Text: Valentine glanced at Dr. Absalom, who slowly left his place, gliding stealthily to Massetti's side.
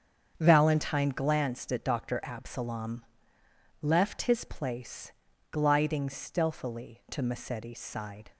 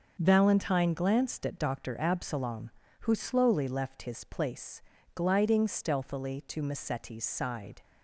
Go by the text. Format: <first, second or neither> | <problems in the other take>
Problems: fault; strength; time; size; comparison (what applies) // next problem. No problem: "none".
second | starts louder than the rest; strong; until 1.3 s; 7.5 dB; also in the second // skips "who slowly"; at 3.4 s